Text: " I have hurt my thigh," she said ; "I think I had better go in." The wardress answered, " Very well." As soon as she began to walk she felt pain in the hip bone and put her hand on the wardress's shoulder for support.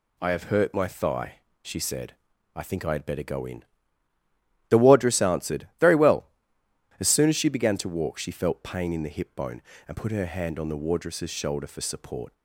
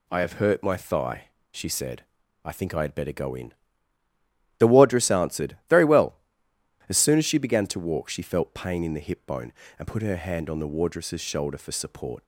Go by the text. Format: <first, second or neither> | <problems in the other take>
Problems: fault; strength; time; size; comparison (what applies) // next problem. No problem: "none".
neither | none